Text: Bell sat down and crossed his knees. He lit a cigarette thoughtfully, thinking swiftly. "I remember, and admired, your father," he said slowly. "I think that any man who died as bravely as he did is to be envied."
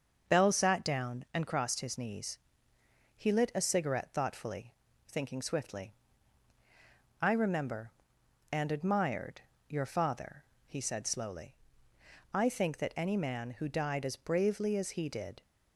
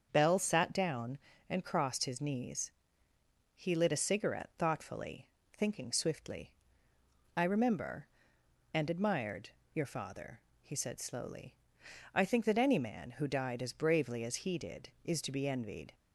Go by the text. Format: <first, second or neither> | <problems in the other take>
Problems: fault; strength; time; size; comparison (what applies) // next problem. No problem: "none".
second | starts louder than the rest; until 1.4 s; 6.5 dB; also in the second // stops before "is to be envied"; at 15.4 s